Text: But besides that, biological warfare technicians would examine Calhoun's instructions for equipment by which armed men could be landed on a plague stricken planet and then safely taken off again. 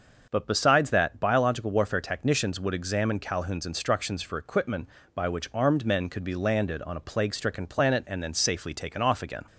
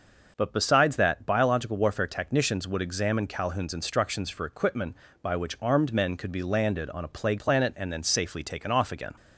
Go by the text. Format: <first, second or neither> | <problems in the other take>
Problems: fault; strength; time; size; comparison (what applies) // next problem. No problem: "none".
first | starts louder than the rest; until 1.3 s; 6 dB; also in the first // skips "stricken"; at 7.3 s